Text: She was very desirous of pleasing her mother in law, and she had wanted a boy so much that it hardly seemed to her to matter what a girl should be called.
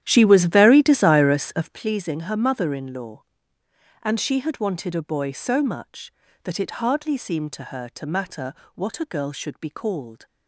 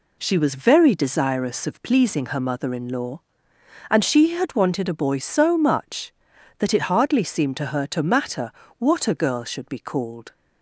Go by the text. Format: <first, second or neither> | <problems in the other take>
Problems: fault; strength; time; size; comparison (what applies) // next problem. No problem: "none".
second | starts louder than the rest; strong; until 1.9 s; 11.5 dB // pauses between "matter" and "what"; slight; at 8.5 s; 0.20 s long; slight in the second